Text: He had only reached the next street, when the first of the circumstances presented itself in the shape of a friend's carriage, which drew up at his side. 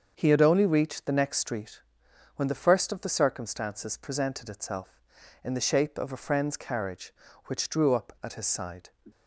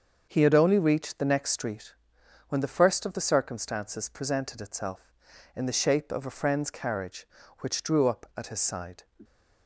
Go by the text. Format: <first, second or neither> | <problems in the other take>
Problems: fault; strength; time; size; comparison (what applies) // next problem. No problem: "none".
neither | starts louder than the rest; the same in both